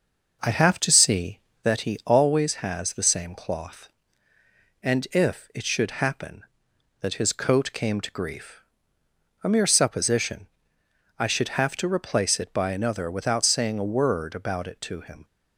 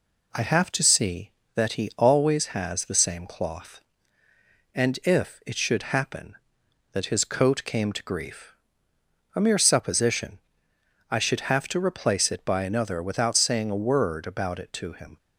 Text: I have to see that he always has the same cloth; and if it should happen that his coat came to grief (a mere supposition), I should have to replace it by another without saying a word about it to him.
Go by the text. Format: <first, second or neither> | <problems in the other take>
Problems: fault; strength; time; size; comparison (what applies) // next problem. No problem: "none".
second | starts louder than the rest; noticeable; until 1.9 s; 6 dB